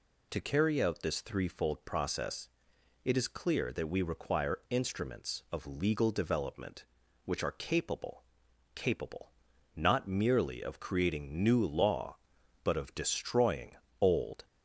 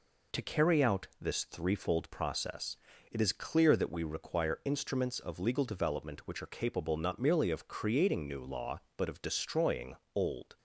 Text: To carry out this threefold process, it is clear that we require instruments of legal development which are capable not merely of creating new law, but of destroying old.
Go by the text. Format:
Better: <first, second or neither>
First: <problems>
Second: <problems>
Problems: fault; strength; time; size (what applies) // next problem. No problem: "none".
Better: second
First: says "capable" twice; at 8.7 s // pauses between "destroying" and "old"; slight; at 13.7 s; 0.24 s long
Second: pauses between "destroying" and "old"; slight; at 9.9 s; 0.19 s long